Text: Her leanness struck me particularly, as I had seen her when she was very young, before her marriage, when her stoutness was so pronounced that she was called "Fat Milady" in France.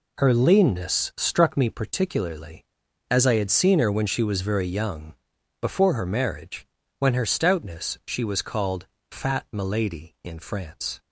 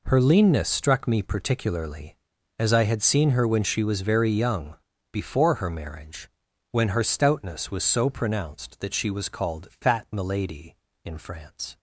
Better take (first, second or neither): second